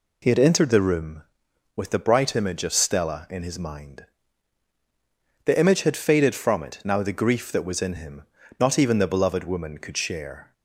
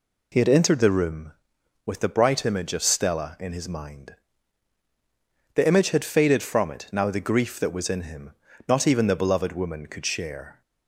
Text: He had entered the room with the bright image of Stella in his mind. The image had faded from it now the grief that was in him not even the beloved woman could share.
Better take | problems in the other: neither | pauses between "him" and "not"; slight; the same in both

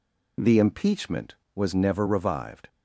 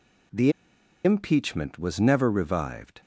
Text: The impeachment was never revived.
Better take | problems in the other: first | pauses between "The" and "impeachment"; noticeable; at 0.5 s; 0.53 s long

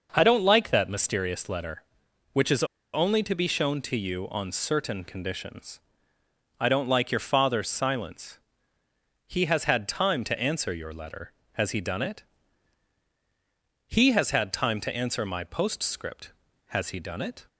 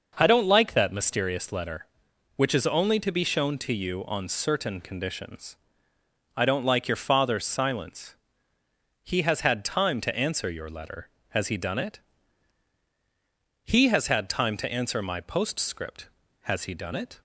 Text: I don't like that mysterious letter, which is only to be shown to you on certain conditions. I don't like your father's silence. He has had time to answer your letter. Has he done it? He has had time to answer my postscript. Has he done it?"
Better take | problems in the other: second | pauses between "is" and "only"; slight; at 2.6 s; 0.29 s long

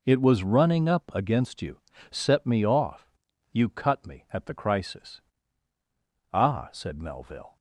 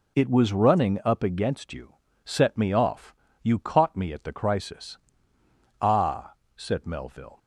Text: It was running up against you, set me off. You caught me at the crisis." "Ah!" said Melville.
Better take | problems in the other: second | says "cut" for "caught"; at 3.6 s

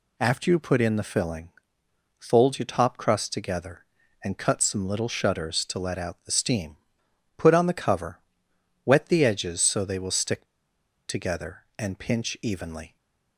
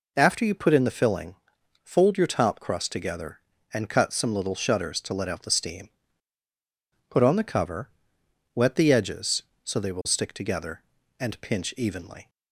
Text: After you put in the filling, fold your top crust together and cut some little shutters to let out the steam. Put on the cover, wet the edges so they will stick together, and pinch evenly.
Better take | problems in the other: second | pauses between "stick" and "together"; noticeable; at 10.4 s; 0.61 s long // stays silent after the last word; slight; from 12.8 s on; 0.5 s long

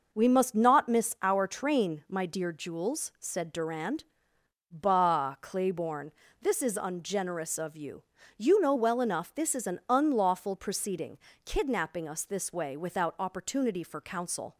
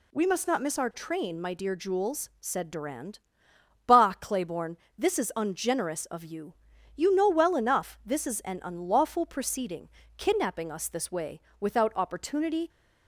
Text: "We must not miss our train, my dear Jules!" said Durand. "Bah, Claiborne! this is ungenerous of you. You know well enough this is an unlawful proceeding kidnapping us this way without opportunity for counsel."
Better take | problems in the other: first | pauses between "proceeding" and "kidnapping"; slight; at 9.8 s; 0.30 s long; slight in the first // pauses between "way" and "without"; slight; at 11.3 s; 0.22 s long // stops before "for counsel"; at 12.7 s

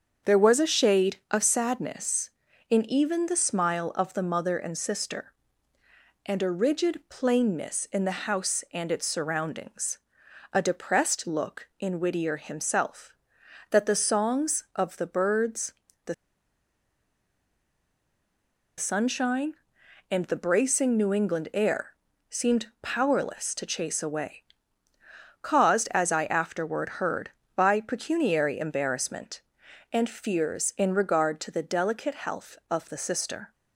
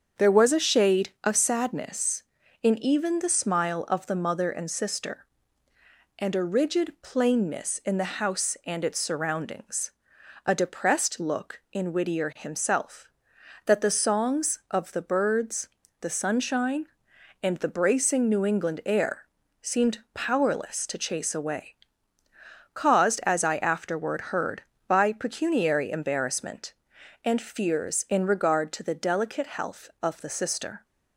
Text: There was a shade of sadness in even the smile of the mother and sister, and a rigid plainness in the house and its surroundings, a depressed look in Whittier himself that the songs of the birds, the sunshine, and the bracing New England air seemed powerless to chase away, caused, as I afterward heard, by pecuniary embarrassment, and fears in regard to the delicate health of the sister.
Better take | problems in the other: second | starts louder than the rest; until 1.4 s; 7 dB; also in the second // pauses between "the" and "sunshine"; strong; at 16.1 s; 2.6 s long // pauses between "air" and "seemed"; slight; at 21.9 s; 0.34 s long; slight in the second // pauses between "seemed" and "powerless"; slight; at 22.6 s; 0.16 s long; slight in the second

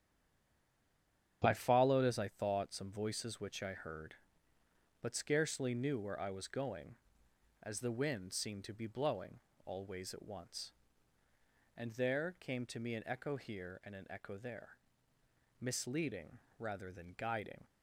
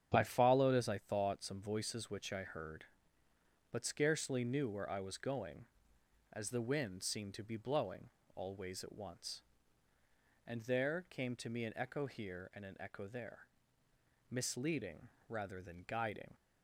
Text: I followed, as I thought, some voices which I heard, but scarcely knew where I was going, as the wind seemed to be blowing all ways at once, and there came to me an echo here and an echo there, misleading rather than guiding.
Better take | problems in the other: second | stays silent before the first word; noticeable; until 1.4 s; 1.4 s long // starts louder than the rest; strong; until 2.4 s; 8.5 dB; strong in the second // pauses between "blowing" and "all"; slight; at 9.3 s; 0.26 s long; slight in the second // pauses between "misleading" and "rather"; slight; at 16.3 s; 0.20 s long; slight in the second

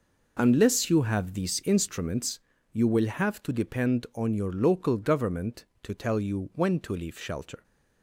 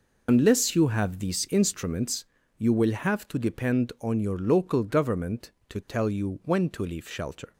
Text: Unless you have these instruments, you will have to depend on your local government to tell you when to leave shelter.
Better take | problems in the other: first | loses the start of "Unless"; at 0.2 s; 65 ms

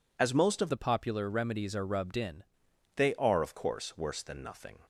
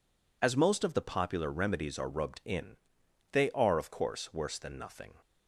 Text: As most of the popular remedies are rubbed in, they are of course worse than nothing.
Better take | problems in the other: second | changes voice from "the" to "in"; from 0.7 to 2.4 s; 1.7 s long

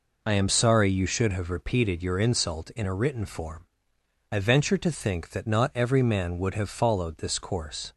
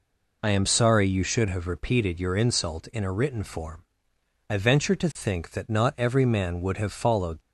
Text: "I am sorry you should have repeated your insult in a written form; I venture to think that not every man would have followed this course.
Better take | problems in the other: first | stops before "this course"; at 7.4 s

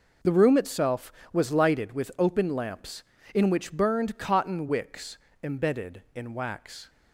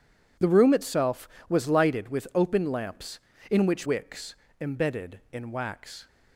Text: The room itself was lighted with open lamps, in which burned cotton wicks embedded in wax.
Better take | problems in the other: first | skips "burned cotton"; at 3.8 s // pauses between "wicks" and "embedded"; slight; at 4.3 s; 0.24 s long; slight in the first

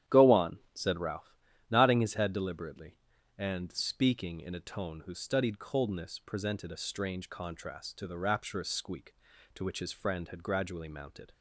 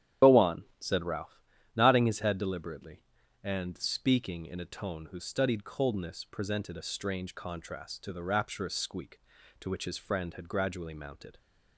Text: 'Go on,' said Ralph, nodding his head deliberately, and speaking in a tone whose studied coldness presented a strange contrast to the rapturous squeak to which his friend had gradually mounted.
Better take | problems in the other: first | loses the start of "Go"; at 0.2 s; 85 ms // starts louder than the rest; strong; until 1.3 s; 10 dB; strong in the first

